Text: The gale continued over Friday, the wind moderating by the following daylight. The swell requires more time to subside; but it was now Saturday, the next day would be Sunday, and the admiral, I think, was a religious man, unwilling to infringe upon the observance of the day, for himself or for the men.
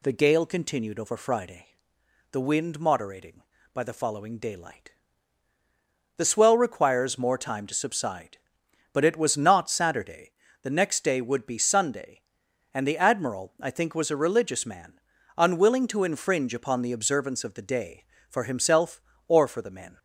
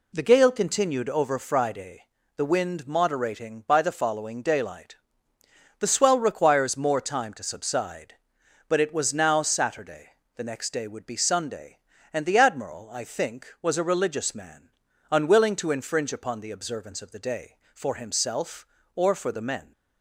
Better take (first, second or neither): second